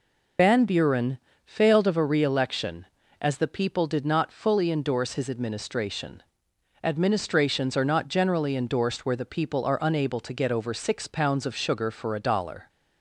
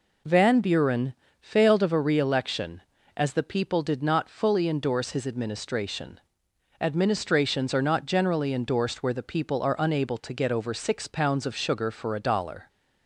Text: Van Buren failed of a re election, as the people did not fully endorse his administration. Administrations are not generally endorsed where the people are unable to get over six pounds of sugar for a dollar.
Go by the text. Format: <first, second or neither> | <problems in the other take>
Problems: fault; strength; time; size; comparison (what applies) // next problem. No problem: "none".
second | loses the start of "Van"; at 0.3 s; 95 ms // pauses between "Buren" and "failed"; slight; at 1.1 s; 0.26 s long; slight in the second